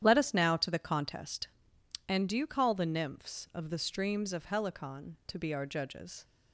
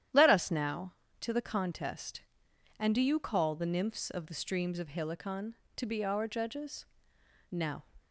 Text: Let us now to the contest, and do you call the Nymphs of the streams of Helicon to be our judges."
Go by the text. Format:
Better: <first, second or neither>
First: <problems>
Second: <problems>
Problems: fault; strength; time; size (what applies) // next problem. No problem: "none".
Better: first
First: starts louder than the rest; strong; until 1.0 s; 10 dB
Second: starts louder than the rest; strong; until 1.4 s; 10.5 dB // goes on to say "Now"; slight; from 7.5 s on; 0.32 s long